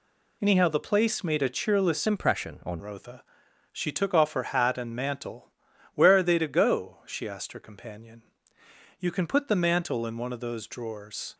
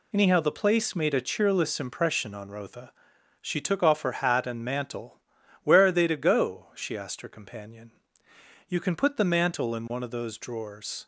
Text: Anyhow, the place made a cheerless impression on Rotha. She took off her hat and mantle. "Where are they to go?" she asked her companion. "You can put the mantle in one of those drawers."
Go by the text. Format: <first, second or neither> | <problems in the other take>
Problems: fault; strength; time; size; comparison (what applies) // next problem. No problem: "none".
second | changes voice from "impression" to "on"; from 2.0 to 2.8 s; 0.8 s long